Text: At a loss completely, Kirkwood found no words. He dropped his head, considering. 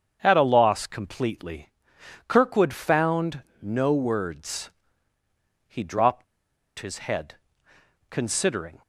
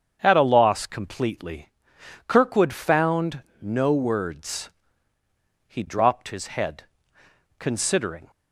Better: second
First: starts louder than the rest; strong; until 1.2 s; 7.5 dB // pauses between "found" and "no"; slight; at 3.4 s; 0.20 s long // pauses between "dropped" and "his"; noticeable; at 6.2 s; 0.54 s long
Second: starts louder than the rest; strong; until 1.2 s; 7.5 dB // pauses between "found" and "no"; slight; at 3.4 s; 0.20 s long

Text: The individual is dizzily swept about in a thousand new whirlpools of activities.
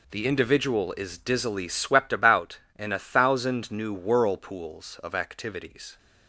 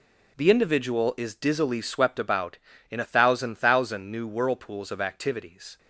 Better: first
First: none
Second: says "thousand" twice; at 3.5 s

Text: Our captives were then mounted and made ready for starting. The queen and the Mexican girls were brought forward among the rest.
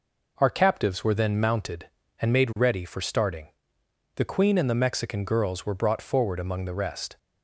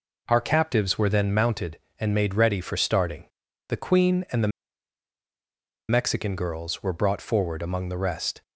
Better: first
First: none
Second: pauses between "the" and "Mexican"; strong; at 4.5 s; 1.3 s long

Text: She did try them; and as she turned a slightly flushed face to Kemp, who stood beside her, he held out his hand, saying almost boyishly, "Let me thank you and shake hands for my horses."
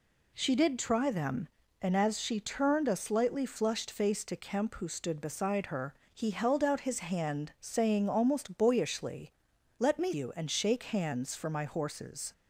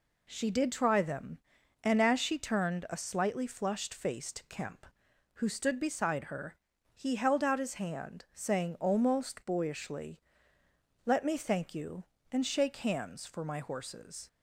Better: second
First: skips "thank"; at 10.1 s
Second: none

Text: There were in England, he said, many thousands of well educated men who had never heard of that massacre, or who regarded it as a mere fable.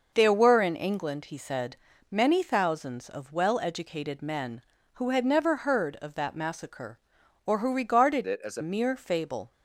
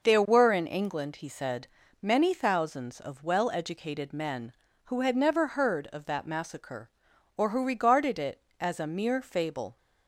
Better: second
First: changes voice from "it" to "a"; from 8.2 to 8.6 s; 0.4 s long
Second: none

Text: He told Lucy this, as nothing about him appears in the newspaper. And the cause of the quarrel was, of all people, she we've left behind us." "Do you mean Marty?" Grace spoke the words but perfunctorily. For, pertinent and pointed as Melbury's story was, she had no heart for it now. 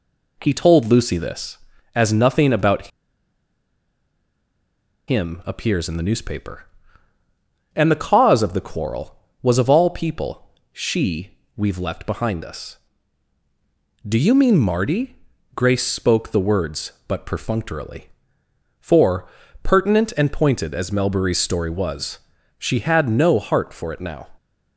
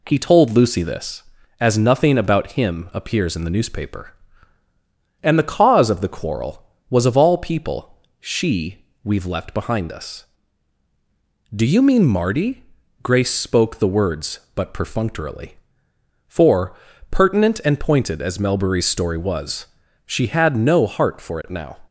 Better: second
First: pauses between "about" and "him"; strong; at 2.8 s; 2.2 s long // pauses between "she" and "we've"; slight; at 11.3 s; 0.26 s long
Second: pauses between "she" and "we've"; slight; at 8.7 s; 0.26 s long

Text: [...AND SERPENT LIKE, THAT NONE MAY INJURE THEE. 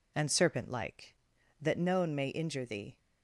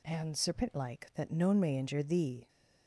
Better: neither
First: none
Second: none

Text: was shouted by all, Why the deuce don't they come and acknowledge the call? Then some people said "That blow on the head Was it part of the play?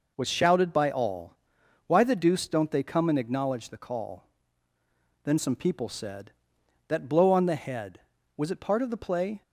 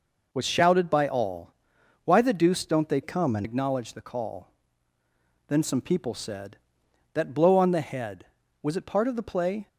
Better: first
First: none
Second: changes voice from "come" to "and"; from 3.0 to 3.4 s; 0.4 s long

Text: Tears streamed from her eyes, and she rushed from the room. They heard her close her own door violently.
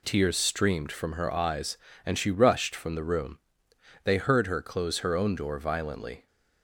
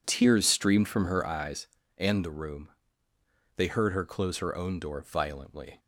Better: first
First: none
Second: skips "she rushed from"; at 2.2 s

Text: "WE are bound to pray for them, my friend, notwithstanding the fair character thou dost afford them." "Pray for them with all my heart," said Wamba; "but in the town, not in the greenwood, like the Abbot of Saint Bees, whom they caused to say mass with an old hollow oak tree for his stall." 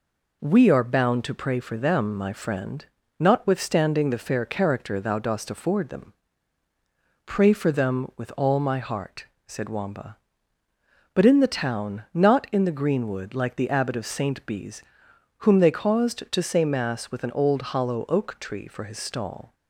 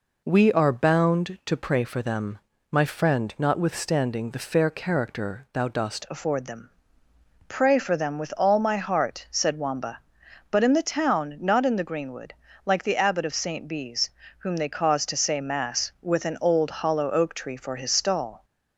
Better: first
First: none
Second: changes voice at "afford"; from 6.1 s on; 12.3 s long

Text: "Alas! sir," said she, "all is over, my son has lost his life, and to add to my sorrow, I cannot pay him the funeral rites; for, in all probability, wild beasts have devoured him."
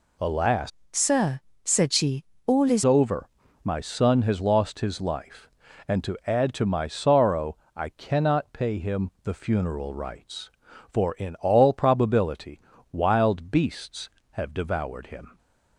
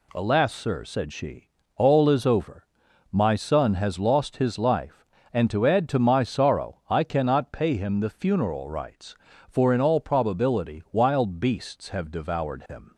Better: second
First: changes voice from "sir" to "is"; from 0.8 to 2.8 s; 2.0 s long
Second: none

